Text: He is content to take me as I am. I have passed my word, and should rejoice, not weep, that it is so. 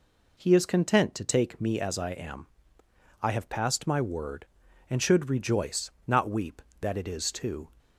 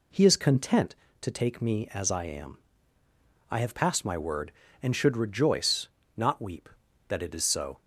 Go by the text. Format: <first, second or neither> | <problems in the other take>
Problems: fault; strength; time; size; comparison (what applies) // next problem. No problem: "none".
second | says "too" for "so"; at 7.3 s